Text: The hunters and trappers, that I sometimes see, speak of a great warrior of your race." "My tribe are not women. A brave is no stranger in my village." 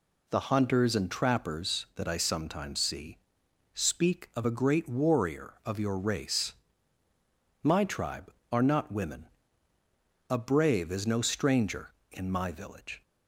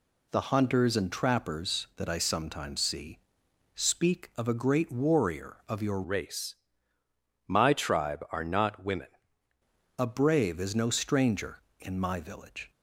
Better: first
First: none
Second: changes voice from "race" to "women"; from 6.0 to 9.0 s; 3.0 s long

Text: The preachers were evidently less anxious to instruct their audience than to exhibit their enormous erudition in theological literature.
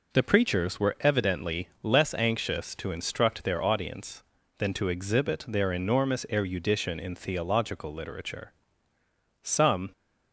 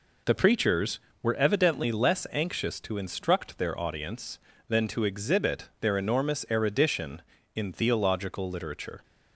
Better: second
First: goes on to say "Some"; slight; from 9.4 s on; 0.48 s long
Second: none

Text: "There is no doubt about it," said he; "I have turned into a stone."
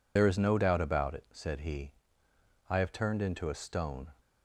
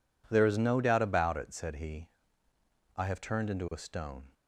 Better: second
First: loses the start of "There"; at 0.1 s; 55 ms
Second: none

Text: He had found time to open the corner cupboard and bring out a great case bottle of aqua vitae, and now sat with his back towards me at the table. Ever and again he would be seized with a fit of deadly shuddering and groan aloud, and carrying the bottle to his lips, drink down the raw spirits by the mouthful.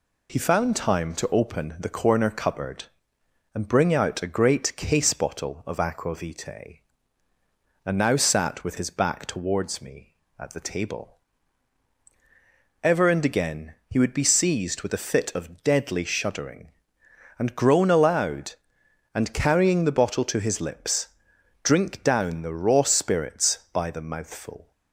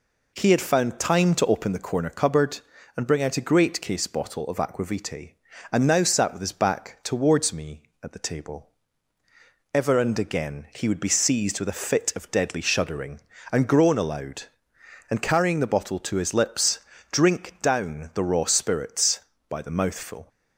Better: second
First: skips "had"; at 0.3 s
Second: none

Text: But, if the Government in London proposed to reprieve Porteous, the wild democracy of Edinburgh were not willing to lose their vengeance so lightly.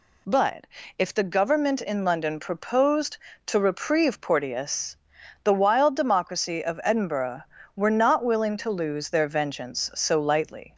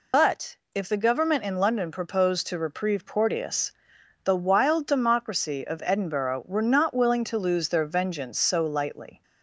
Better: first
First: none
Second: loses the start of "But"; at 0.1 s; 155 ms

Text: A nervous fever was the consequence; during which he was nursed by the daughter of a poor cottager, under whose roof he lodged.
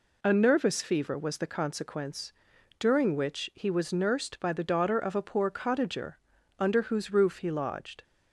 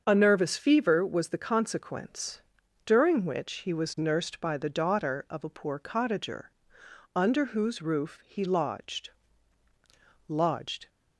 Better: first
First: none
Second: starts louder than the rest; until 1.0 s; 6.5 dB // says "lodged" twice; at 10.2 s

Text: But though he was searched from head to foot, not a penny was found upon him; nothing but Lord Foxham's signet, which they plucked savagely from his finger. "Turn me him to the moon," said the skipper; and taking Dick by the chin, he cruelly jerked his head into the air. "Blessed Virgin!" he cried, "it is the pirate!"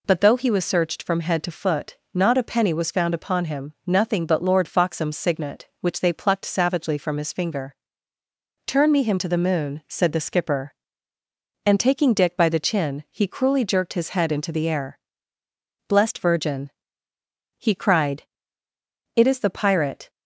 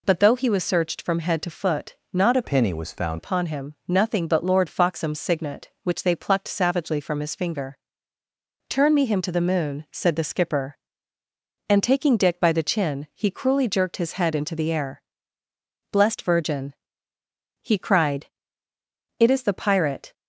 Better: first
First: none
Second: changes voice from "penny" to "found"; from 2.4 to 3.1 s; 0.7 s long

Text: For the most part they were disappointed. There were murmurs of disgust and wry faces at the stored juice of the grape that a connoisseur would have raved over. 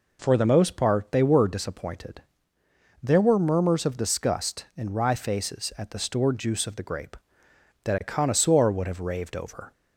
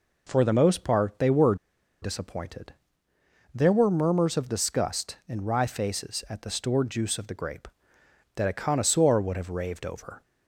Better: first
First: none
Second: pauses between "were" and "disappointed"; noticeable; at 1.5 s; 0.46 s long

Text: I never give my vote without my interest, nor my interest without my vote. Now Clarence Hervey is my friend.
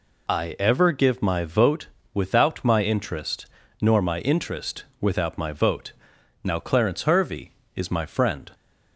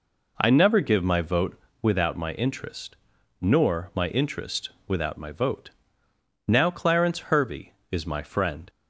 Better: second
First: says "ever" for "never"; at 0.5 s // pauses between "vote" and "without"; slight; at 1.8 s; 0.26 s long // pauses between "interest" and "without"; slight; at 4.8 s; 0.18 s long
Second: pauses between "vote" and "without"; slight; at 1.5 s; 0.24 s long // pauses between "interest" and "without"; slight; at 4.6 s; 0.18 s long

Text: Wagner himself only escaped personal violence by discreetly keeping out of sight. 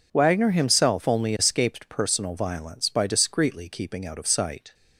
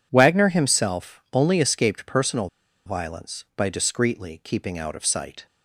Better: first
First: none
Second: pauses between "personal" and "violence"; at 2.4 s; 0.37 s long

